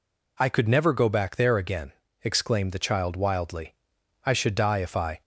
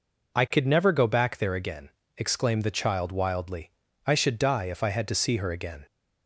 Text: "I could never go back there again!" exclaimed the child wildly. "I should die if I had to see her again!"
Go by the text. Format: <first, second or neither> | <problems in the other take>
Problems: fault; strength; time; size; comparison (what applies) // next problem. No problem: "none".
second | stops before "had to see her again"; at 5.2 s